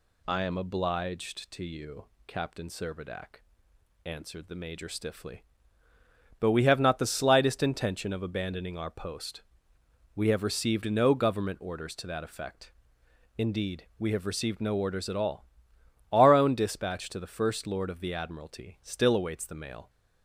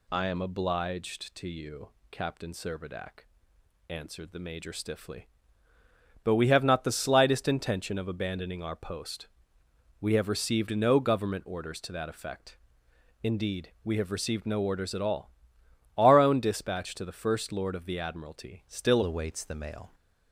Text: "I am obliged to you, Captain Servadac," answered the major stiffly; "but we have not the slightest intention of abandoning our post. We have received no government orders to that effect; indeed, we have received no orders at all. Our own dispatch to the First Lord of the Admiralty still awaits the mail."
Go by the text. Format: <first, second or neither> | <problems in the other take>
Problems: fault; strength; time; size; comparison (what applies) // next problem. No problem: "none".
first | changes voice at "awaits"; from 19.0 s on; 0.9 s long